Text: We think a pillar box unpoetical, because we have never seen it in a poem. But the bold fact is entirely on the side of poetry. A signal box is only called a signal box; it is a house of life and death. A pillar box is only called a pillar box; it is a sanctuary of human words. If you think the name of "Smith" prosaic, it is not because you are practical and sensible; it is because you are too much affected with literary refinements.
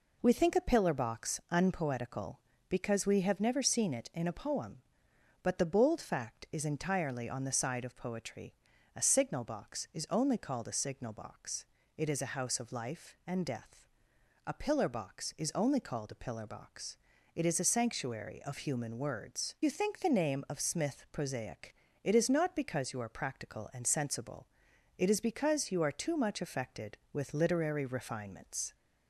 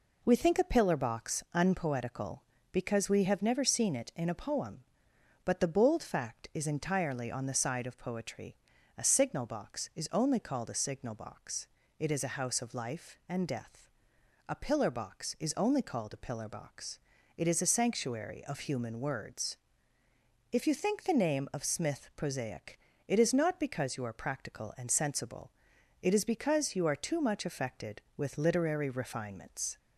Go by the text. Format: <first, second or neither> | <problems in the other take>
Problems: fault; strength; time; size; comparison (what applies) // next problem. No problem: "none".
second | skips "If"; at 19.5 s